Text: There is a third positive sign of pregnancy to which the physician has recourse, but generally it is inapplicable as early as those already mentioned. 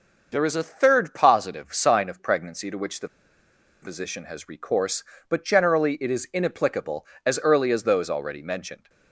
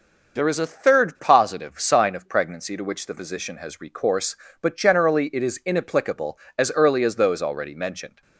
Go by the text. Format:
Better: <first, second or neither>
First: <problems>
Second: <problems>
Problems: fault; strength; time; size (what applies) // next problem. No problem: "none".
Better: second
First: starts louder than the rest; noticeable; until 1.3 s; 6 dB // pauses between "the" and "physician"; noticeable; at 3.0 s; 0.75 s long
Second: starts louder than the rest; noticeable; until 1.4 s; 6 dB